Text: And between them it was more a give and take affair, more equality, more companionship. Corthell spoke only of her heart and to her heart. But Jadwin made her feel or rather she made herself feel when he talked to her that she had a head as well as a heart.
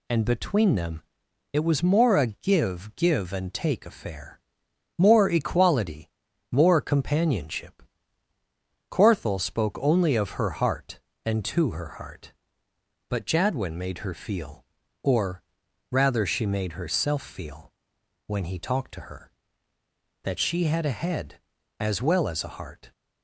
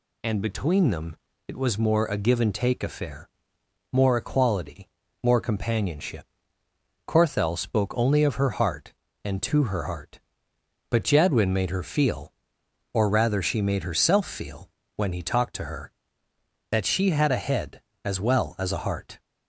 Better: second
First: pauses between "them" and "it"; noticeable; at 1.0 s; 0.50 s long // says "give" twice; at 2.9 s // pauses between "or" and "rather"; noticeable; at 15.4 s; 0.50 s long // pauses between "feel" and "when"; noticeable; at 17.7 s; 0.54 s long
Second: pauses between "them" and "it"; slight; at 1.1 s; 0.30 s long // pauses between "feel" and "when"; slight; at 14.7 s; 0.26 s long

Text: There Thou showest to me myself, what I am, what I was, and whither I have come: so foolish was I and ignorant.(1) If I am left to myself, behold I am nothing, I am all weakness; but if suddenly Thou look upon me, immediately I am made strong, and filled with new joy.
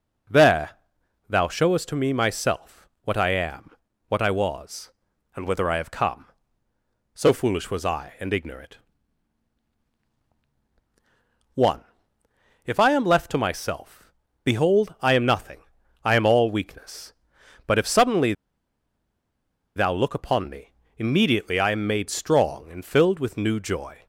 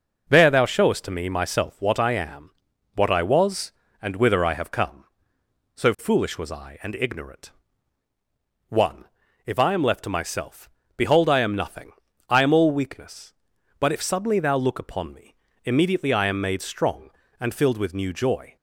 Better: second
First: starts louder than the rest; strong; until 1.8 s; 9.5 dB // pauses between "There" and "Thou"; noticeable; at 0.7 s; 0.56 s long // pauses between "suddenly" and "Thou"; strong; at 18.3 s; 1.4 s long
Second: none

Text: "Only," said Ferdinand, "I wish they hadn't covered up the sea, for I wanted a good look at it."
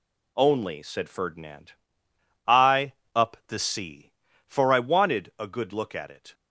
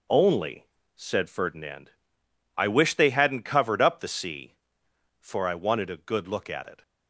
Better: second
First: skips "wish they hadn't covered"; at 3.0 s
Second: none

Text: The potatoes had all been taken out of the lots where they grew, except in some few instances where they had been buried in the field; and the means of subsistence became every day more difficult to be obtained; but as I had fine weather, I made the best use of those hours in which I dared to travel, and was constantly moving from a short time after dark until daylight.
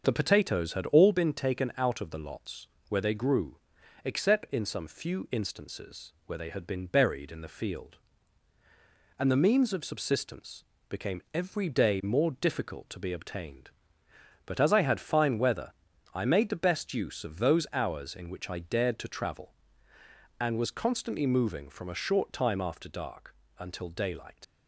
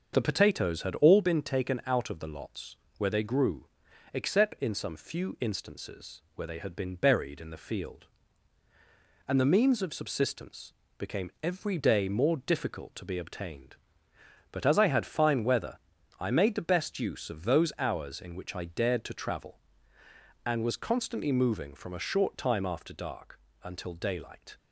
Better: second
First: starts louder than the rest; until 1.0 s; 6.5 dB // pauses between "lots" and "where"; slight; at 2.6 s; 0.22 s long // pauses between "subsistence" and "became"; slight; at 10.6 s; 0.26 s long // pauses between "dark" and "until"; slight; at 23.3 s; 0.24 s long // leaves "daylight" unfinished; at 24.4 s; 85 ms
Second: starts louder than the rest; until 1.1 s; 6.5 dB // pauses between "lots" and "where"; slight; at 2.7 s; 0.22 s long // pauses between "subsistence" and "became"; slight; at 10.7 s; 0.26 s long // pauses between "dark" and "until"; slight; at 23.3 s; 0.24 s long

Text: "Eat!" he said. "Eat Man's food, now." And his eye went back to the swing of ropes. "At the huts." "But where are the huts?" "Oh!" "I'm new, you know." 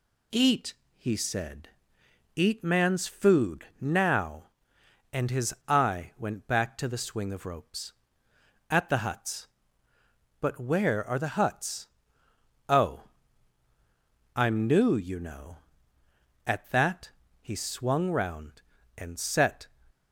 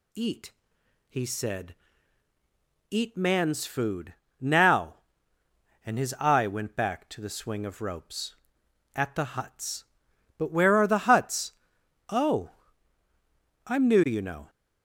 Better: second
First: pauses between "his" and "eye"; slight; at 5.5 s; 0.15 s long // goes on to say "At that he swung round and set"; strong; from 16.4 s on; 3.2 s long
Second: none

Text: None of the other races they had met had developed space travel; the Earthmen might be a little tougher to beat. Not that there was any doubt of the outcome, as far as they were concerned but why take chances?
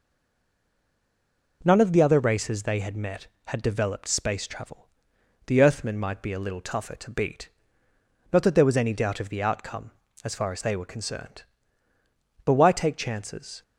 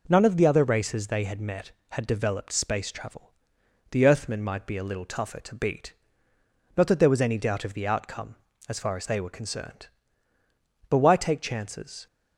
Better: second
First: stays silent before the first word; noticeable; until 1.6 s; 1.6 s long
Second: none

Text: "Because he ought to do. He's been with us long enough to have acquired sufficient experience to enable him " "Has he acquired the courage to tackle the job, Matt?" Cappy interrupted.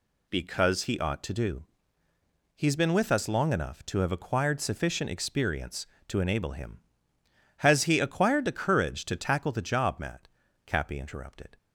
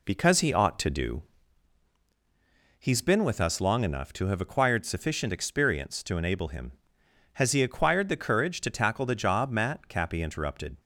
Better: first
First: none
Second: starts louder than the rest; slight; until 1.3 s; 3 dB

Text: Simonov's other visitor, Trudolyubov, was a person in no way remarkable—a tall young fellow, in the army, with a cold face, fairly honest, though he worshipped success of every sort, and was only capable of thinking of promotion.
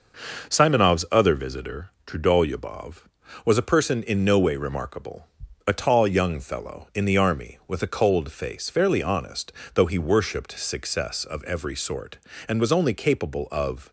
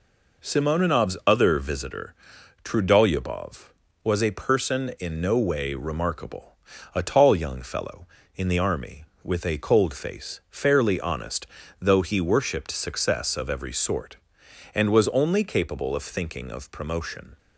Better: second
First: stops before "thinking of promotion"; at 13.8 s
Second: none

